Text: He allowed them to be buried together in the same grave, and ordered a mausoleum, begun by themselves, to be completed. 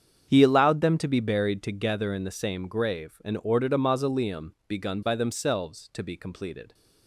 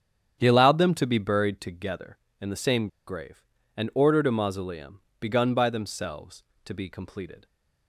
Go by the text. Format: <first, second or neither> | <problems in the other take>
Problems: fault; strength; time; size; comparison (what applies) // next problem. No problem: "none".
first | starts louder than the rest; strong; until 1.4 s; 8.5 dB; strong in the first // pauses between "same" and "grave"; slight; at 2.8 s; 0.19 s long